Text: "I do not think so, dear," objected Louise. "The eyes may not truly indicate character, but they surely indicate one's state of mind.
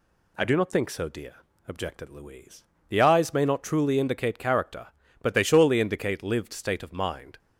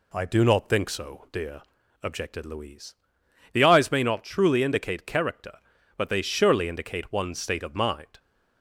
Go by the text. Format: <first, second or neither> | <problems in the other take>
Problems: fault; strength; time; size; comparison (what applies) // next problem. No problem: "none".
second | says "lived" for "one's"; at 6.2 s